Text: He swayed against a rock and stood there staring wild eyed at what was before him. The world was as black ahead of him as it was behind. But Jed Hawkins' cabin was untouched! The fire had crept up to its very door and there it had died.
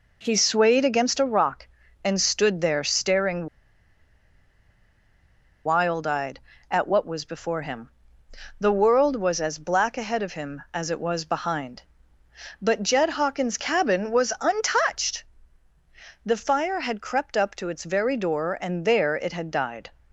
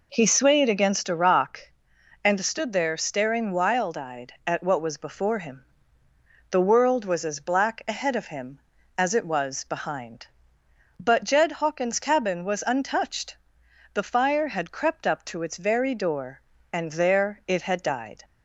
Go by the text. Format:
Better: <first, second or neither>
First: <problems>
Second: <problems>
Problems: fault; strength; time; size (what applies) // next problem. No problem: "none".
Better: second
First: pauses between "staring" and "wild"; strong; at 3.4 s; 2.1 s long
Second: none